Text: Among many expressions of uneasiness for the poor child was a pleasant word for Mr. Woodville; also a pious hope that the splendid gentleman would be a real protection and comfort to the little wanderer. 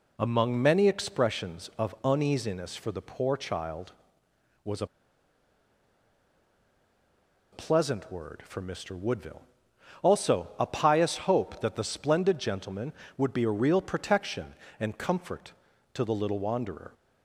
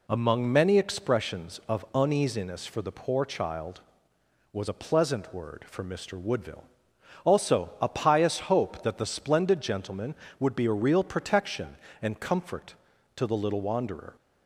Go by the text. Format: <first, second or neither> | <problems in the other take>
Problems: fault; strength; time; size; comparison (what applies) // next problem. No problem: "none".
second | pauses between "a" and "pleasant"; strong; at 4.8 s; 2.6 s long